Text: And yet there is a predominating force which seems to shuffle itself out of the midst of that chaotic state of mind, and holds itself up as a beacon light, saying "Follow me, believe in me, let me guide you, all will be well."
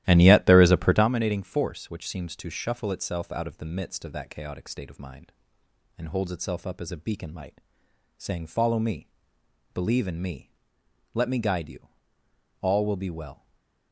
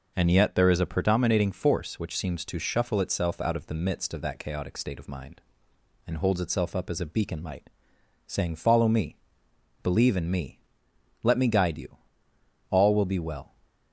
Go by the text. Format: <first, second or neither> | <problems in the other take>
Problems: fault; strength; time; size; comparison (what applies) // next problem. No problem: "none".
second | starts louder than the rest; strong; until 1.1 s; 14 dB // stays silent after the last word; slight; from 13.3 s on; 0.6 s long